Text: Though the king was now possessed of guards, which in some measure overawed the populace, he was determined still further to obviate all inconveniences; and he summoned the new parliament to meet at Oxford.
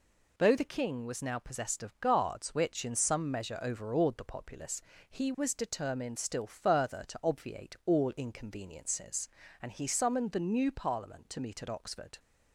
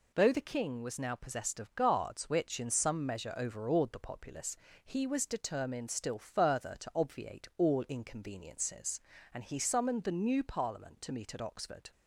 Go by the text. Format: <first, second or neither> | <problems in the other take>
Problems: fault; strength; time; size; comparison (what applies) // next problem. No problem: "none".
neither | none